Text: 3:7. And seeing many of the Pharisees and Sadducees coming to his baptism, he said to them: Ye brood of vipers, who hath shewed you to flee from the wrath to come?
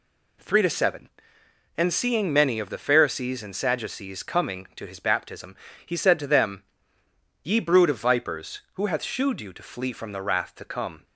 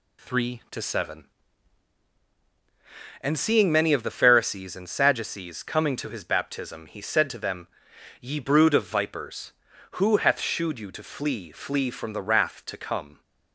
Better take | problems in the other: first | says "flee" twice; at 11.5 s

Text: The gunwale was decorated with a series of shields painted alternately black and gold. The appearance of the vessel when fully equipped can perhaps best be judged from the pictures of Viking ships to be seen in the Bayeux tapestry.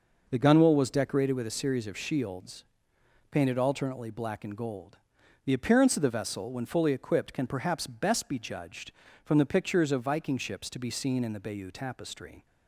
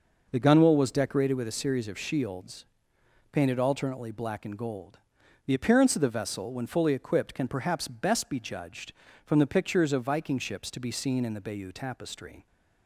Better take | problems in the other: neither | pauses between "shields" and "painted"; noticeable; the same in both

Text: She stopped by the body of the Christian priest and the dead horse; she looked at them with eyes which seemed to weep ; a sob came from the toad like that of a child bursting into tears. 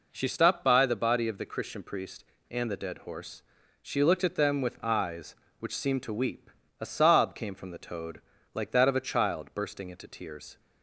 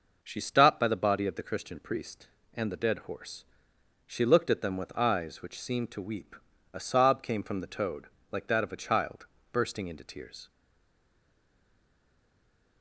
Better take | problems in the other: first | pauses between "toad" and "like"; slight; at 8.0 s; 0.24 s long; slight in the first // pauses between "child" and "bursting"; slight; at 9.2 s; 0.26 s long // stays silent after the last word; from 10.5 s on; 2.3 s long

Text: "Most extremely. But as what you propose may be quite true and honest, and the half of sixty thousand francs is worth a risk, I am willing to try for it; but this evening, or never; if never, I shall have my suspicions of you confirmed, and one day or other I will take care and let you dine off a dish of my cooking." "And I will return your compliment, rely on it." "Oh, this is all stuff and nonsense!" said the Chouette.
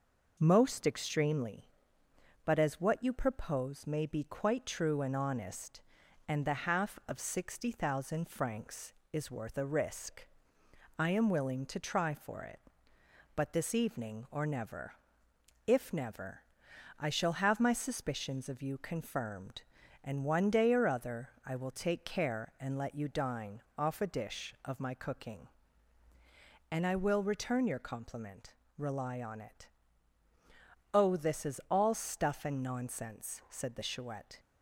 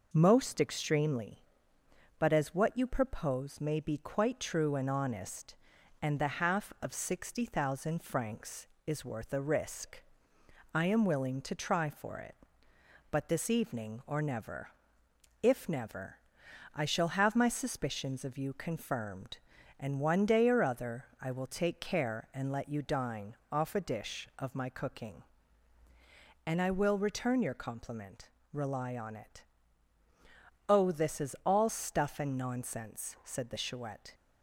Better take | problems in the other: neither | pauses between "other" and "I"; slight; the same in both // pauses between "dine" and "off"; slight; the same in both

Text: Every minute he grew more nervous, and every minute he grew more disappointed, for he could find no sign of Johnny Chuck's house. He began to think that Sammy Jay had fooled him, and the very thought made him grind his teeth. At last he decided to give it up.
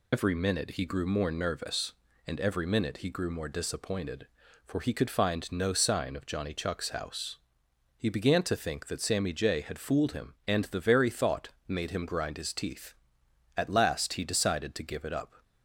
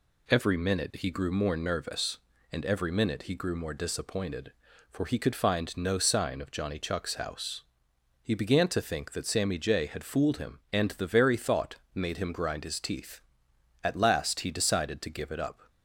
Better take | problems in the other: second | loses the start of "Every"; at 0.1 s; 70 ms // pauses between "thought" and "made"; slight; at 11.4 s; 0.20 s long; slight in the second

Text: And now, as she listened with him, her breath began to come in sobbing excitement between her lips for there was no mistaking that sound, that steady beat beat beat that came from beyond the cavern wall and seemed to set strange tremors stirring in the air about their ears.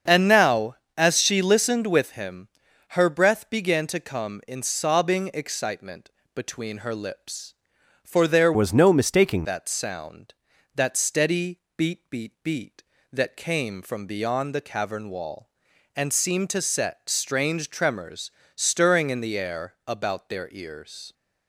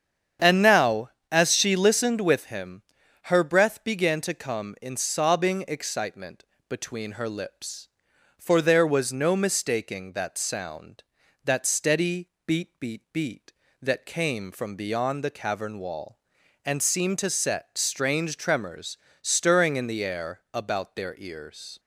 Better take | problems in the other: second | starts louder than the rest; strong; until 1.2 s; 7 dB; strong in the second // pauses between "excitement" and "between"; slight; at 6.1 s; 0.22 s long; slight in the second // changes voice from "was" to "mistaking"; from 8.5 to 9.4 s; 0.9 s long // pauses between "steady" and "beat"; slight; at 11.5 s; 0.20 s long; slight in the second // pauses between "tremors" and "stirring"; slight; at 18.2 s; 0.28 s long; slight in the second

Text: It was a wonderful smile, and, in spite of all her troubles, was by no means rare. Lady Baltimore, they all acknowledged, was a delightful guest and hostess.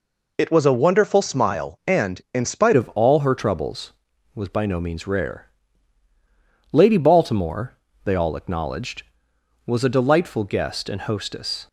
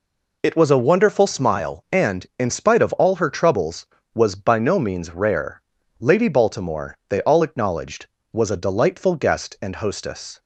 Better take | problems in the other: second | changes voice at "of"; from 2.7 s on; 8.9 s long

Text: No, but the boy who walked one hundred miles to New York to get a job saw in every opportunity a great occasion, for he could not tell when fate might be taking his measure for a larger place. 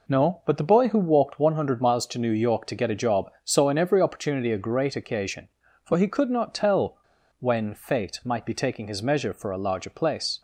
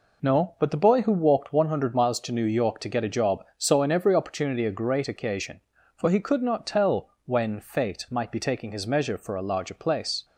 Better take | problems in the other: second | pauses between "tell" and "when"; at 6.9 s; 0.40 s long

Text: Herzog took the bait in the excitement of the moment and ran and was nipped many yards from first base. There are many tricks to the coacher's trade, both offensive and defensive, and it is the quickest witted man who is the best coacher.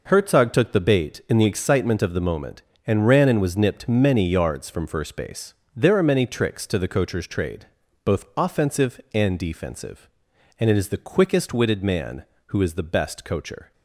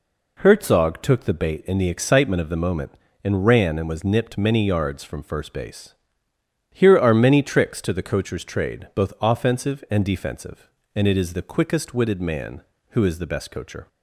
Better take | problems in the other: first | says "Here" for "There"; at 6.6 s

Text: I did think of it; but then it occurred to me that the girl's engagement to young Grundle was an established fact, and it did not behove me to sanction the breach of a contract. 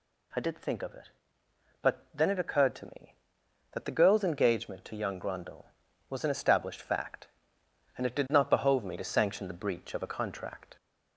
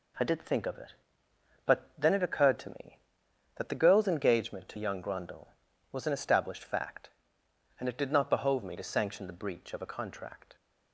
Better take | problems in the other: second | gets louder; slight; throughout; 2 dB

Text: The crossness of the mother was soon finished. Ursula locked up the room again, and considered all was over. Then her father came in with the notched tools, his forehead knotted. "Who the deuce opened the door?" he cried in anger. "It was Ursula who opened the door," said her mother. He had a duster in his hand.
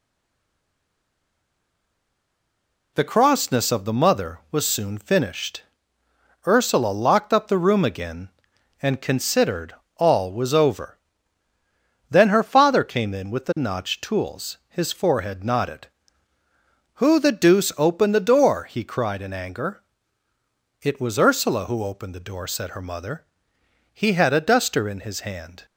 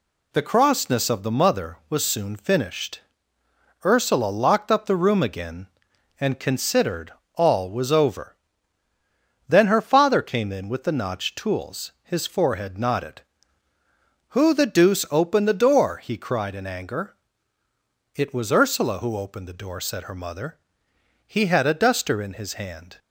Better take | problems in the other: second | stays silent before the first word; strong; until 2.9 s; 2.9 s long // pauses between "considered" and "all"; slight; at 9.7 s; 0.22 s long; slight in the second

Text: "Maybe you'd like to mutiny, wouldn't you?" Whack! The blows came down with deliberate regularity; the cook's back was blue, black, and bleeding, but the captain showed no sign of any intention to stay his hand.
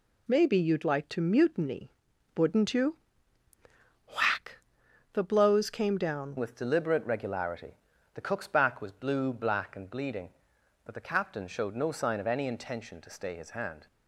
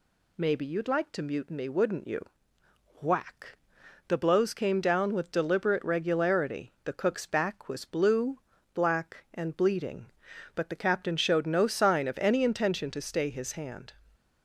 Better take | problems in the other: second | changes voice at "with"; from 6.3 s on; 7.5 s long

